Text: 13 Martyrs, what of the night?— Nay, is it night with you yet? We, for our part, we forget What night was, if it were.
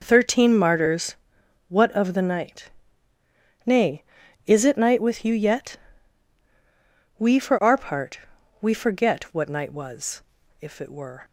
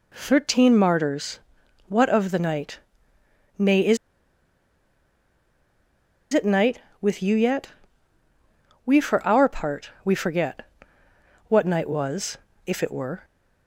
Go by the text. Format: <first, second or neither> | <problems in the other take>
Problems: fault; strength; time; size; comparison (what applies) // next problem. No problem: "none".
first | pauses between "is" and "it"; strong; at 3.9 s; 2.3 s long // pauses between "forget" and "What"; noticeable; at 10.6 s; 0.86 s long